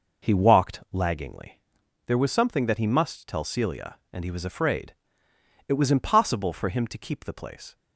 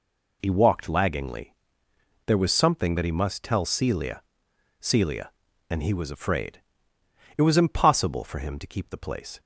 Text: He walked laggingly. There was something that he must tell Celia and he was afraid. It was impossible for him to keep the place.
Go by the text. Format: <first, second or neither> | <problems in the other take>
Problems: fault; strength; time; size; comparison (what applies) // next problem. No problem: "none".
first | says "Celia" twice; at 4.7 s